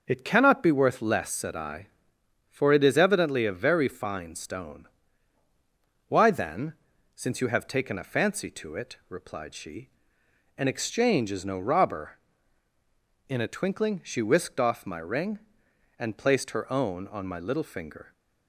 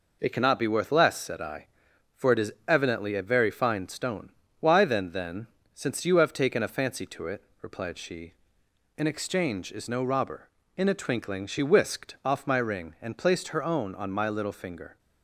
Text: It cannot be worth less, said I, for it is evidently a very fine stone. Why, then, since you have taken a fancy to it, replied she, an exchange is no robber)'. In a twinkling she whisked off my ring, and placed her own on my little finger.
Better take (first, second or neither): first